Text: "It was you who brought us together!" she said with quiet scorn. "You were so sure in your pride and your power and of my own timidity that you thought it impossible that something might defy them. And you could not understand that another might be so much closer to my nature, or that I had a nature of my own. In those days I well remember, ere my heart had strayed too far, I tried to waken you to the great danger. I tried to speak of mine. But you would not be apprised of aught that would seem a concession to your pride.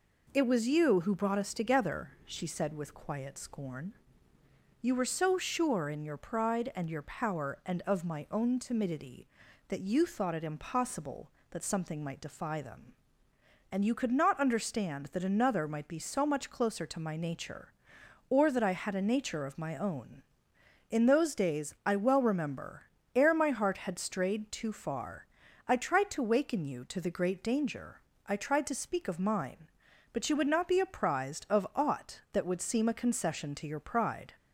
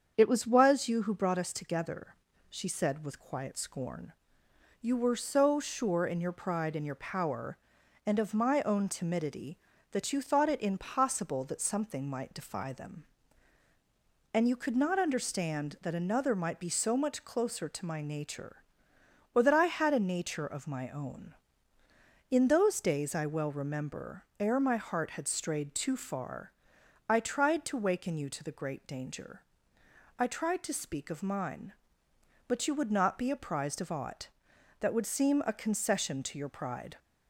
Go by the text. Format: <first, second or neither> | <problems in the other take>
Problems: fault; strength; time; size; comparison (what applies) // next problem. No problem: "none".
first | starts louder than the rest; strong; until 1.1 s; 7 dB // says "was" twice; at 0.4 s